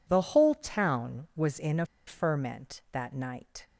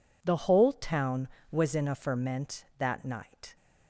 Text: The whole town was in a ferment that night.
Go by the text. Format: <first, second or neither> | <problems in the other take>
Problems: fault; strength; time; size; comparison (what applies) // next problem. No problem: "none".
second | pauses between "a" and "ferment"; slight; at 1.8 s; 0.21 s long